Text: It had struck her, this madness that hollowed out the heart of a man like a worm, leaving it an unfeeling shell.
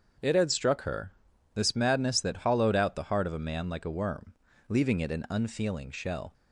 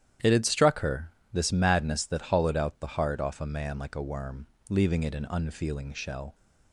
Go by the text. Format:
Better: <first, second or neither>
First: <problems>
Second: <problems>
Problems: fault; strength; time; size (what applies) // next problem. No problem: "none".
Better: first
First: starts louder than the rest; until 1.6 s; 7 dB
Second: starts louder than the rest; strong; until 1.4 s; 11 dB // says "off" for "of"; at 3.1 s